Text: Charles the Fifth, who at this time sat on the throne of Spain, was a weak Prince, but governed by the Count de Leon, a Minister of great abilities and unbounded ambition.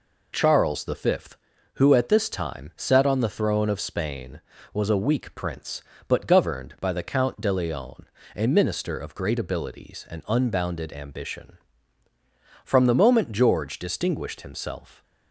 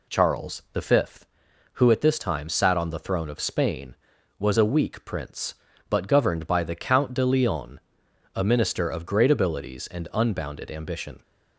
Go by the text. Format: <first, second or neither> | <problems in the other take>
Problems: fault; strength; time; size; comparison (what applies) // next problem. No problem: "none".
second | goes on to say "From the moment George distinguished himself"; strong; from 12.6 s on; 2.3 s long